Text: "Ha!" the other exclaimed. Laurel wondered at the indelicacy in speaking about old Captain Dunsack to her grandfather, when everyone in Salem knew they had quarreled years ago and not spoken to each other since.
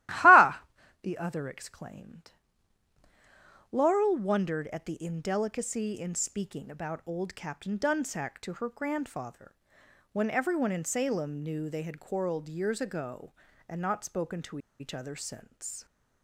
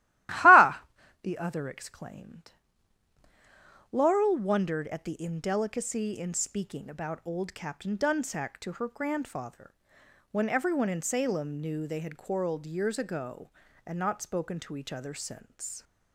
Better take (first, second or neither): second